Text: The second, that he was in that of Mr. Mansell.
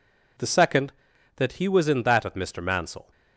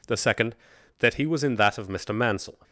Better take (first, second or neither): neither